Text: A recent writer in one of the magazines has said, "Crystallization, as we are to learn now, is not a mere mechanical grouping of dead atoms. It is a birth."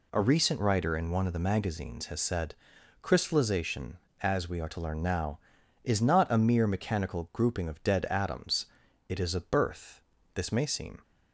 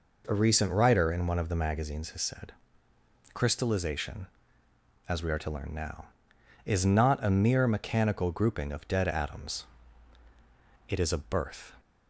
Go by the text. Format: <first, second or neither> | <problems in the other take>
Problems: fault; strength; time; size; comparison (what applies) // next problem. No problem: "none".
second | goes on to say "This may seem"; noticeable; from 10.3 s on; 0.68 s long